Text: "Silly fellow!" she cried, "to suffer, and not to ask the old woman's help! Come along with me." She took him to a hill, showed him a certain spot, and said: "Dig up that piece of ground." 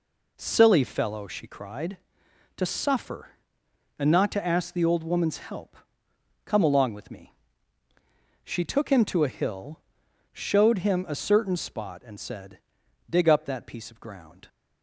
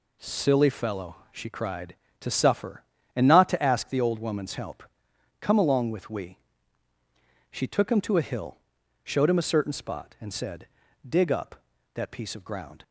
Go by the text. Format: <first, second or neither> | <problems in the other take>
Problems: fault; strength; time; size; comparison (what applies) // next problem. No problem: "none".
first | says "we" for "me"; at 6.1 s